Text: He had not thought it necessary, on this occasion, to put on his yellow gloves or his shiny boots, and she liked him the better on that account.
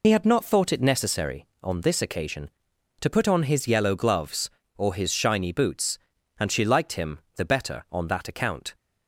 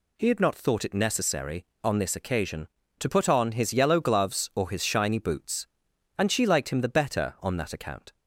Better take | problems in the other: second | loses the start of "He"; at 0.0 s; 45 ms // pauses between "him" and "the"; slight; at 7.1 s; 0.18 s long

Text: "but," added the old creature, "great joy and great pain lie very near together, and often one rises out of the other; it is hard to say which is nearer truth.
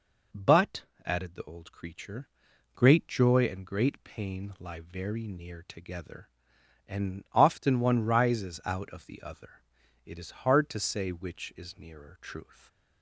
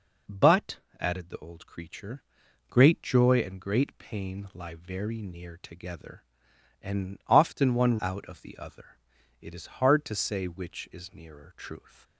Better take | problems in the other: first | skips "rises"; at 7.9 s

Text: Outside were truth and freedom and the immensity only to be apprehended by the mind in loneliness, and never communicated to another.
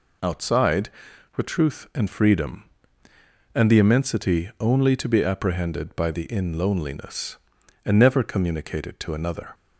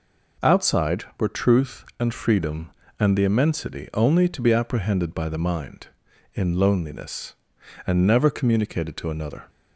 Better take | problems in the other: second | skips "mind"; at 6.2 s

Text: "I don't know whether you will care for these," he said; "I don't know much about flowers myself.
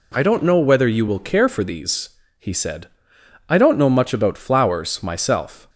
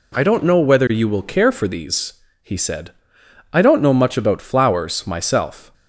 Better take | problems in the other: neither | none

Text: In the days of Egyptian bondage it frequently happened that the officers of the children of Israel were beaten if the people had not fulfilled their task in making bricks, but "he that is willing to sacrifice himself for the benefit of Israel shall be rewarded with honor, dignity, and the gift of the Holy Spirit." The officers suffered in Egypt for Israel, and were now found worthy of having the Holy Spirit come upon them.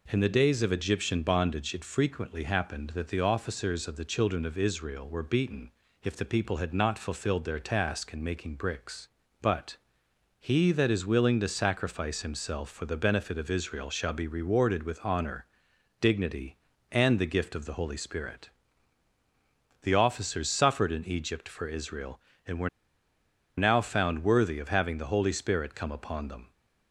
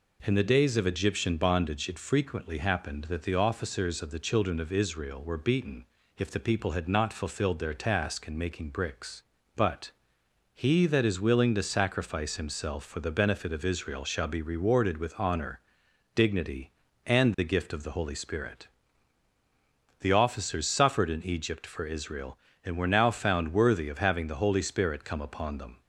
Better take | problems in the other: second | pauses between "beaten" and "if"; slight; at 5.7 s; 0.34 s long; slight in the second // pauses between "but" and "he"; noticeable; at 9.7 s; 0.64 s long; noticeable in the second // pauses between "were" and "now"; noticeable; at 22.6 s; 0.88 s long

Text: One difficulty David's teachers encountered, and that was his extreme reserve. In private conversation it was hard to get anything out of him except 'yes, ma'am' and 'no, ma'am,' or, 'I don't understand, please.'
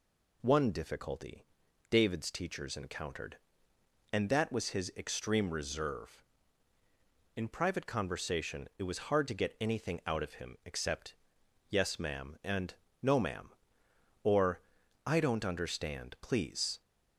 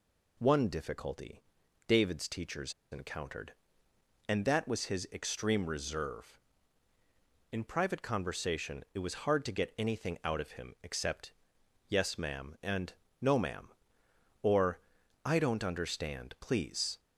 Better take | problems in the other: first | pauses between "difficulty" and "David's"; at 1.4 s; 0.44 s long; also in the first // pauses between "teachers" and "encountered"; slight; at 2.7 s; 0.18 s long // pauses between "except" and "yes"; noticeable; at 11.3 s; 0.56 s long; noticeable in the first // pauses between "and" and "no"; slight; at 12.9 s; 0.26 s long; slight in the first

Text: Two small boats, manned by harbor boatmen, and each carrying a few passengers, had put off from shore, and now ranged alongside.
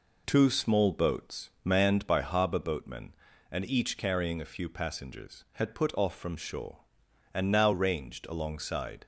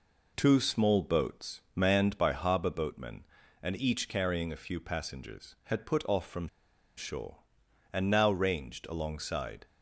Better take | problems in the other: first | pauses between "from" and "shore"; noticeable; at 6.4 s; 0.51 s long

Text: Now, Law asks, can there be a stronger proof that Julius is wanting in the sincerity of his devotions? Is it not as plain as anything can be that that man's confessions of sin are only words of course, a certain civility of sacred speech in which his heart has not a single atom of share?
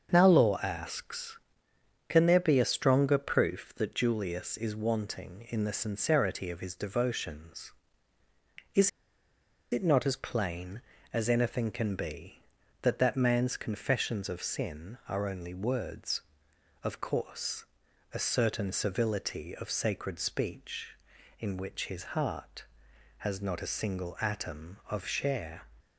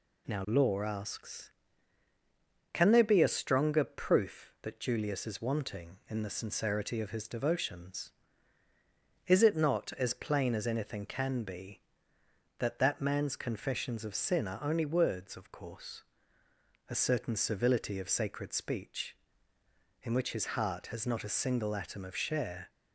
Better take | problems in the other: second | starts louder than the rest; until 1.1 s; 7 dB // pauses between "Is" and "it"; noticeable; at 8.8 s; 0.82 s long

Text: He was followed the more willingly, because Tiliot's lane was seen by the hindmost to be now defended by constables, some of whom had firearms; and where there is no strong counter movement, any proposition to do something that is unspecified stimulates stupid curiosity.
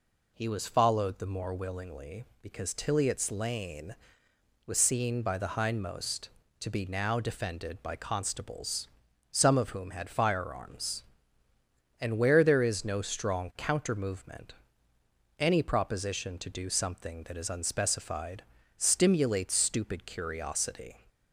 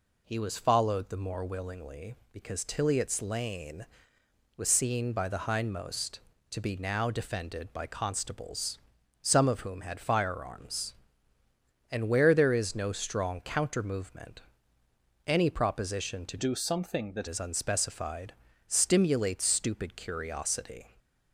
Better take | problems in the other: first | changes voice from "do" to "that"; from 16.3 to 17.2 s; 0.9 s long // pauses between "unspecified" and "stimulates"; slight; at 18.3 s; 0.32 s long; slight in the first

